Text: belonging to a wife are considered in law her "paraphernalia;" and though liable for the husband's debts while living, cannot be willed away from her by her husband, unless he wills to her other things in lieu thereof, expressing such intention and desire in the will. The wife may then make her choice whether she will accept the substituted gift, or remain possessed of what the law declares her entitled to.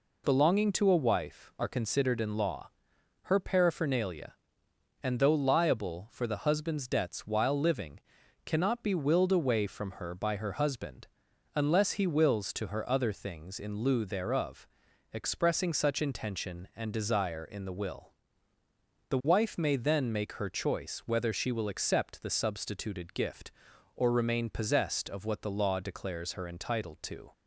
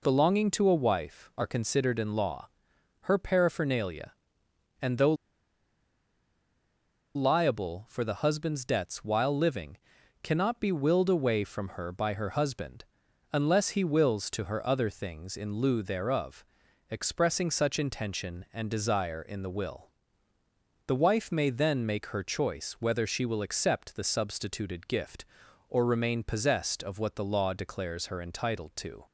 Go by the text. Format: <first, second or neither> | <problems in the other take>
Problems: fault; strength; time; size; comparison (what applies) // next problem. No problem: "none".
first | pauses between "law" and "her"; noticeable; at 2.4 s; 0.54 s long; noticeable in the first // pauses between "though" and "liable"; strong; at 5.1 s; 2.0 s long